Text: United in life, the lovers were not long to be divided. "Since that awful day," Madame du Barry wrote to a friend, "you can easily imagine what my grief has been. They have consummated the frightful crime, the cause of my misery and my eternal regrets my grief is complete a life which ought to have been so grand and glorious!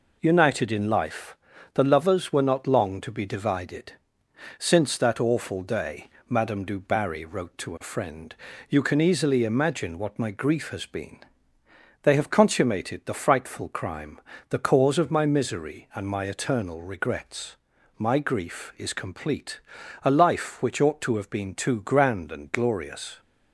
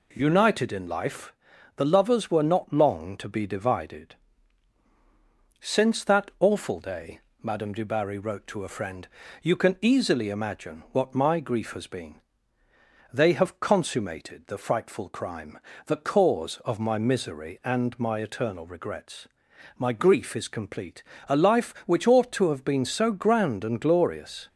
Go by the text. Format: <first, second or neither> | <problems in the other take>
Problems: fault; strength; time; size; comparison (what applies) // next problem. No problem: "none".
second | pauses between "regrets" and "my"; at 17.5 s; 0.42 s long; noticeable in the second // pauses between "complete" and "a"; at 19.5 s; 0.44 s long; slight in the second // says "too" for "so"; at 21.5 s